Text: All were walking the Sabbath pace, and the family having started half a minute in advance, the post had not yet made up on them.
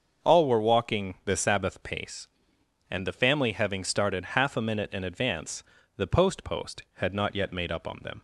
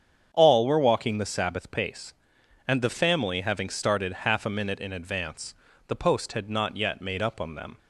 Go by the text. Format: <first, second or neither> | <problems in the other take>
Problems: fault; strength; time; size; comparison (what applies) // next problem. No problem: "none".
second | starts louder than the rest; until 1.3 s; 6.5 dB; strong in the second // says "post" twice; at 6.4 s